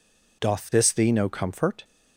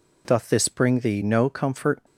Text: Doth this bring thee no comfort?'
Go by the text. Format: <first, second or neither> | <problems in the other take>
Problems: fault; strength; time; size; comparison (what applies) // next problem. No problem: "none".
second | skips "bring"; at 0.9 s